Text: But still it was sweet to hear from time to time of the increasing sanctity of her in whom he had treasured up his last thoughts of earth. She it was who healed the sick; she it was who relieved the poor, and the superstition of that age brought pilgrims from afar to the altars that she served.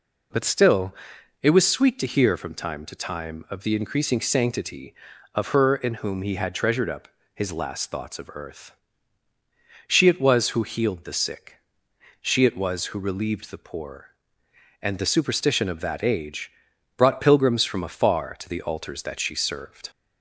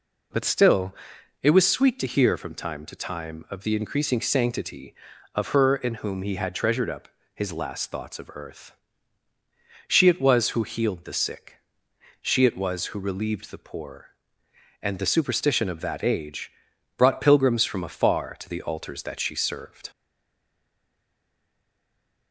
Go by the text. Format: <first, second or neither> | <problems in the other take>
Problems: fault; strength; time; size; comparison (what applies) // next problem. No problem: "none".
first | pauses between "still" and "it"; noticeable; at 0.9 s; 0.46 s long; noticeable in the first // pauses between "up" and "his"; slight; at 7.0 s; 0.28 s long; slight in the first // pauses between "age" and "brought"; noticeable; at 16.5 s; 0.48 s long; noticeable in the first // stays silent after the last word; from 19.9 s on; 2.4 s long